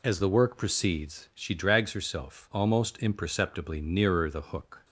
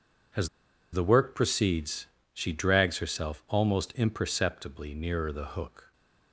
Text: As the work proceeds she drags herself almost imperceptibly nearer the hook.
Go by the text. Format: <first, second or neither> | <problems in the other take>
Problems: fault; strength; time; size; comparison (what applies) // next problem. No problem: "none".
first | pauses between "As" and "the"; at 0.4 s; 0.45 s long // pauses between "proceeds" and "she"; slight; at 2.0 s; 0.24 s long